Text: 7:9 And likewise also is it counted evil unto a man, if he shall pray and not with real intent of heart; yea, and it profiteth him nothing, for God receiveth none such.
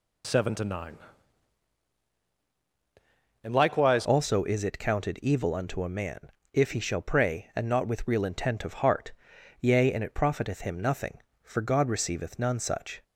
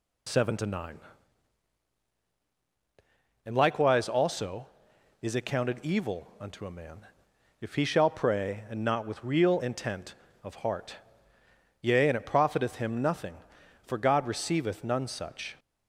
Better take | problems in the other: second | changes voice at "also"; from 4.0 s on; 9.0 s long

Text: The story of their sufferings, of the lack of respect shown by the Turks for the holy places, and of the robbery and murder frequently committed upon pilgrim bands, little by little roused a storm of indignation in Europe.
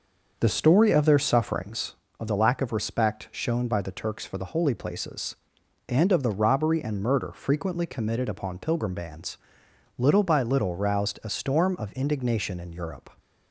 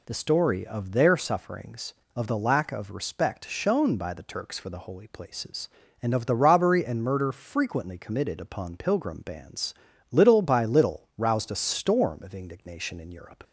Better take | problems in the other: second | starts louder than the rest; until 2.0 s; 6 dB

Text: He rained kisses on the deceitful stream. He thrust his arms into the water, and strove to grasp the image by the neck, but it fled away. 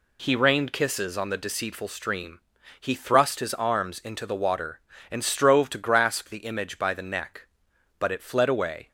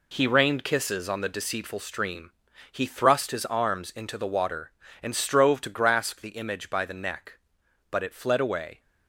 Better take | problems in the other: first | gets quieter; strong; throughout; 7.5 dB

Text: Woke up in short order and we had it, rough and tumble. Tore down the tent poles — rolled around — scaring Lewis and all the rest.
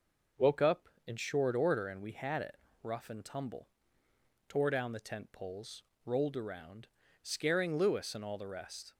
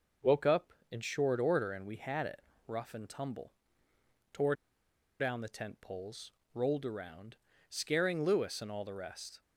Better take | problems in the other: first | pauses between "Tore" and "down"; noticeable; at 4.5 s; 0.66 s long

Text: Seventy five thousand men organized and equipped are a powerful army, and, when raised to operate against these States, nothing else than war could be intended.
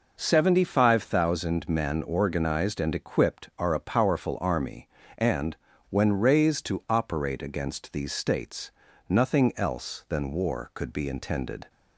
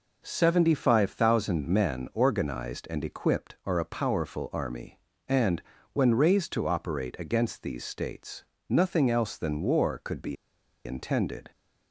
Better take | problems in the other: first | pauses between "be" and "intended"; noticeable; at 10.3 s; 0.51 s long

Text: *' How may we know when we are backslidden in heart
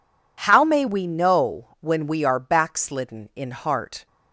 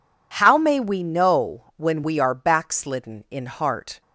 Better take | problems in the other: neither | none

